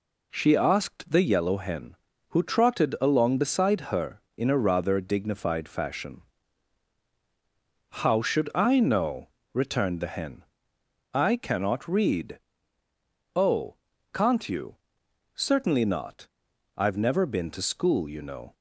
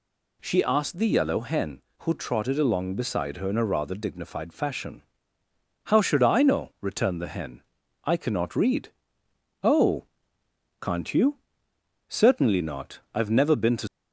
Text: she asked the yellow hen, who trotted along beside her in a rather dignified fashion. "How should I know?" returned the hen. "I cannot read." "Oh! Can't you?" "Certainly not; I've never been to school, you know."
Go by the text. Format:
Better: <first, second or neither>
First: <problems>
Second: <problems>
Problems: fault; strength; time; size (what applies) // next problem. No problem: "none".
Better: first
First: none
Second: stops before "school you know"; at 13.8 s